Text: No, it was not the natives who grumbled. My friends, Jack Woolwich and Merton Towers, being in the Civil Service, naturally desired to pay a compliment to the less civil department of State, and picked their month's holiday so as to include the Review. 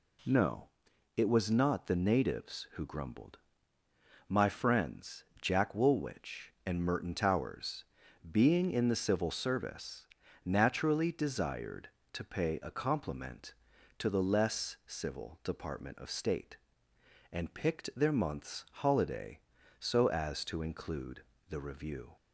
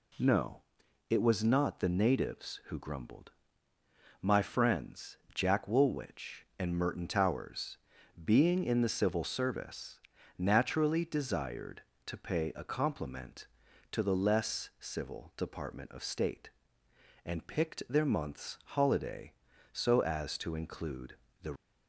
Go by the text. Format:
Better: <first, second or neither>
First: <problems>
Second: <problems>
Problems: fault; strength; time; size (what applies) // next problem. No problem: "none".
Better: first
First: pauses between "include" and "the"; slight; at 21.2 s; 0.26 s long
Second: pauses between "include" and "the"; slight; at 21.1 s; 0.26 s long // stops before "Review"; at 21.5 s